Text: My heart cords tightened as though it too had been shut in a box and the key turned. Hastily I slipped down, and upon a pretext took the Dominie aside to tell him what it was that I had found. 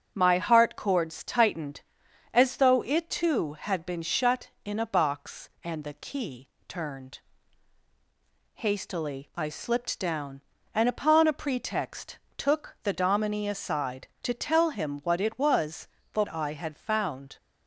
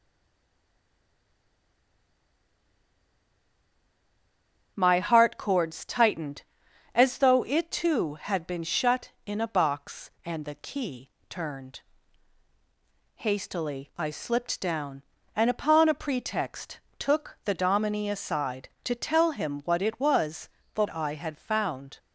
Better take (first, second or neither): first